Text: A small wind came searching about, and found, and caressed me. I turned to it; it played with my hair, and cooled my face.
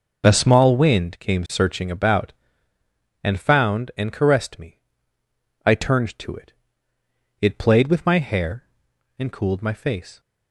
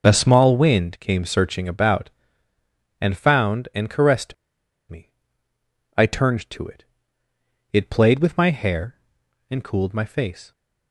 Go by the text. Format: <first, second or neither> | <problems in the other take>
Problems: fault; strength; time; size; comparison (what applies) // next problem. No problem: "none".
first | pauses between "caressed" and "me"; noticeable; at 4.3 s; 0.56 s long